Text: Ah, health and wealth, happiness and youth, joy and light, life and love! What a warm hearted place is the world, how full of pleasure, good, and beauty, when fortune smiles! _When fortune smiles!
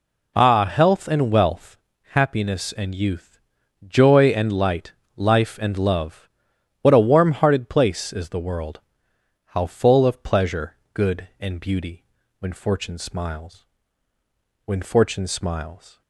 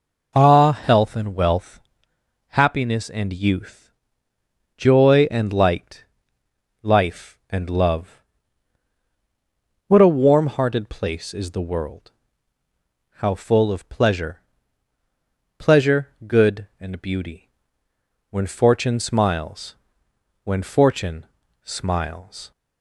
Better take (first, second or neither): first